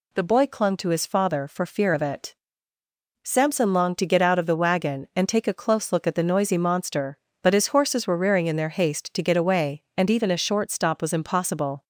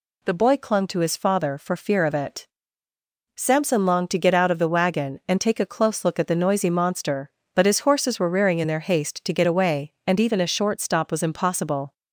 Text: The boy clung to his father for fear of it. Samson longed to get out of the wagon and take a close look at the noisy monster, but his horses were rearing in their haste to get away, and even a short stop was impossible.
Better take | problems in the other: neither | none

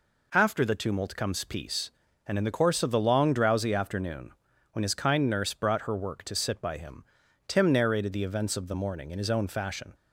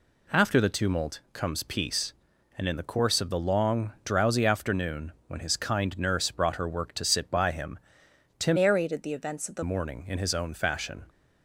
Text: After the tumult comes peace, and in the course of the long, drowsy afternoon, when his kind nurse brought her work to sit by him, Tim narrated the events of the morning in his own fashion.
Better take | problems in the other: first | changes voice from "narrated" to "the"; from 8.5 to 9.6 s; 1.1 s long

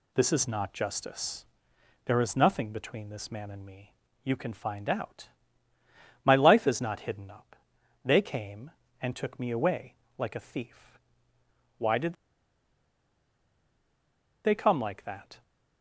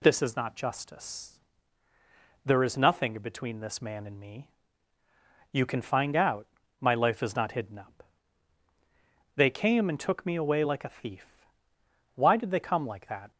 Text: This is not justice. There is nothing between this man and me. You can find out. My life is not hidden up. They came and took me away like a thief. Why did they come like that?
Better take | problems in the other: second | pauses between "away" and "like"; slight; at 9.9 s; 0.24 s long // pauses between "did" and "they"; strong; at 12.1 s; 2.3 s long

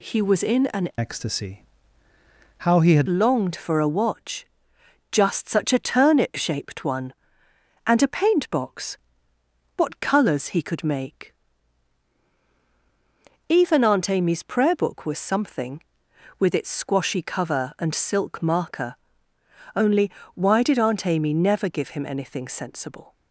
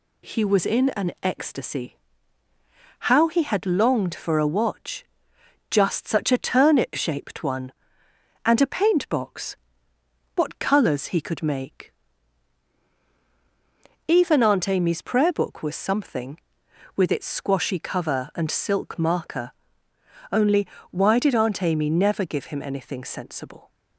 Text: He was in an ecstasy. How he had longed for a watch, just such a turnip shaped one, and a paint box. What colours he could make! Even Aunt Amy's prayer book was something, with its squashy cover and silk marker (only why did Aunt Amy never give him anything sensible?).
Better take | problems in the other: second | changes voice from "ecstasy" to "had"; from 0.9 to 3.0 s; 2.1 s long // pauses between "only" and "why"; slight; at 20.1 s; 0.24 s long; slight in the second

